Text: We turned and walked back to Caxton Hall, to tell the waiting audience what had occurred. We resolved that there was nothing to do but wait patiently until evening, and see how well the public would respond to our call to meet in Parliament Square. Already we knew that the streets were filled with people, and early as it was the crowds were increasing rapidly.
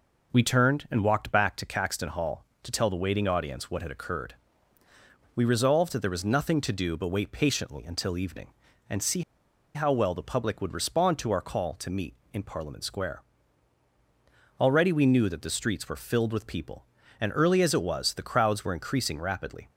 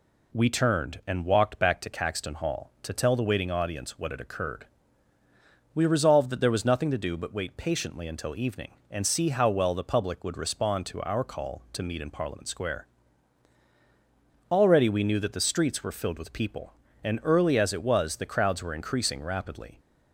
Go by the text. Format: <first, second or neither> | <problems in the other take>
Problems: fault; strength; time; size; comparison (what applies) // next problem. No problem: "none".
second | pauses between "see" and "how"; noticeable; at 9.2 s; 0.52 s long